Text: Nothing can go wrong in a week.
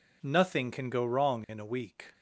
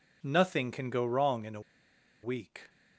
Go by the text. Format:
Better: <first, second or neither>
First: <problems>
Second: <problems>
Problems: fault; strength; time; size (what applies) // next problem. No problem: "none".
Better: first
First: none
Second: pauses between "a" and "week"; noticeable; at 1.6 s; 0.62 s long